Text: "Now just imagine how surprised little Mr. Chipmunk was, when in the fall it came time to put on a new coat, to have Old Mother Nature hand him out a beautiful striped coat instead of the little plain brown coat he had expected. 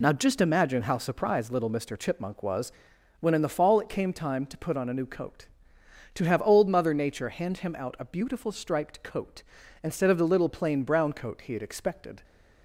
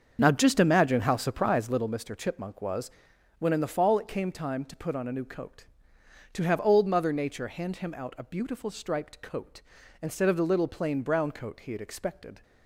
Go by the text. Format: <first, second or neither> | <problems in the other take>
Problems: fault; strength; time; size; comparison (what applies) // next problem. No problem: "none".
first | starts louder than the rest; until 1.9 s; 6.5 dB